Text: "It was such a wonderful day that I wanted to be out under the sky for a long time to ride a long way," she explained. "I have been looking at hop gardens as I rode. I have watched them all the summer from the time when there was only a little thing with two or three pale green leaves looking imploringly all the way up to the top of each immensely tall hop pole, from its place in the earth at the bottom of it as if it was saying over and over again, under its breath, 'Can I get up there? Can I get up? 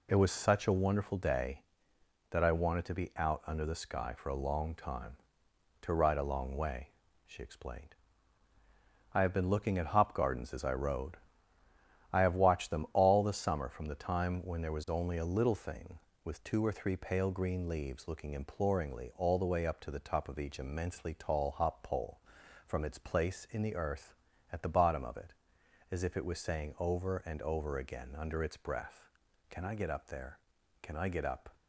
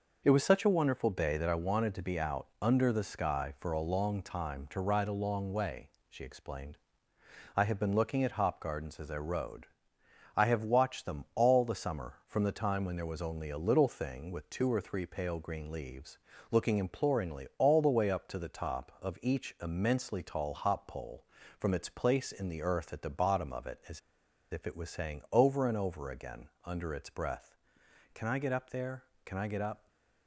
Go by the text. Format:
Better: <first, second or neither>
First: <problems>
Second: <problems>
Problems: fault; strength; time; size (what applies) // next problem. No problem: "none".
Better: first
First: none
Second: pauses between "leaves" and "looking"; slight; at 16.1 s; 0.32 s long // pauses between "as" and "if"; noticeable; at 23.9 s; 0.51 s long // stays silent after the last word; slight; from 29.7 s on; 0.5 s long